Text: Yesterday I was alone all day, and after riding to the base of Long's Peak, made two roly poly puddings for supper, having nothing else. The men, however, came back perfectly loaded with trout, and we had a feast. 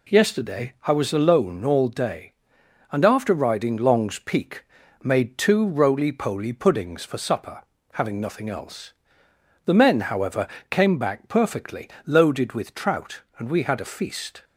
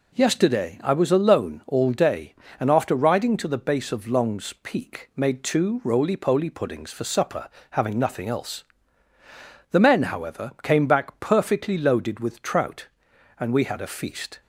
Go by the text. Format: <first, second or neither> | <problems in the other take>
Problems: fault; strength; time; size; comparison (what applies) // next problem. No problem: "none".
second | skips "to the base of"; at 3.7 s // pauses between "perfectly" and "loaded"; slight; at 11.8 s; 0.16 s long